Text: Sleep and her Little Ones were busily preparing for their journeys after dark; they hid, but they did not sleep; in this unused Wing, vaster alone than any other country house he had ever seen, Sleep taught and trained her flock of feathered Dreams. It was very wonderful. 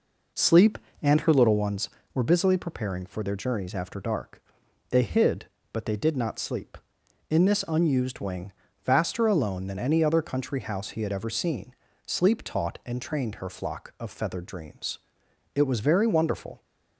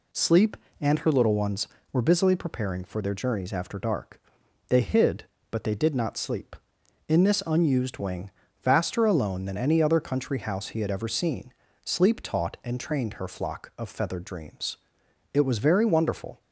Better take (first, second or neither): second